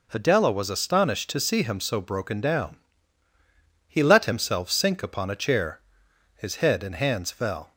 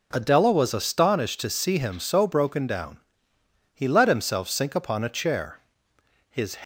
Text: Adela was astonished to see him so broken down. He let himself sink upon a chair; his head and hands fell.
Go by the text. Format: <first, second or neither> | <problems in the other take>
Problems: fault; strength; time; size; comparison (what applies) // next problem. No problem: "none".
first | stops before "head and hands fell"; at 6.6 s